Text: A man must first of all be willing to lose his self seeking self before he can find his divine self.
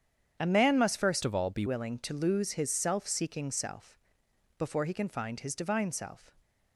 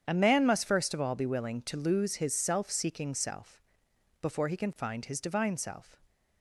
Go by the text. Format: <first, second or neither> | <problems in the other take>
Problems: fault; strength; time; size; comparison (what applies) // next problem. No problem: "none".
second | starts louder than the rest; strong; until 1.4 s; 8.5 dB; strong in the second // changes voice from "of" to "be"; from 1.2 to 1.6 s; 0.4 s long // pauses between "self" and "before"; noticeable; at 3.9 s; 0.58 s long; noticeable in the second